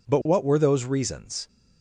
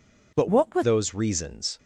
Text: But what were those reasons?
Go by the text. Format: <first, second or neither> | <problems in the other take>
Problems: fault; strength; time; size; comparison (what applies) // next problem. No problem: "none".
first | changes voice from "what" to "were"; from 0.4 to 0.8 s; 0.4 s long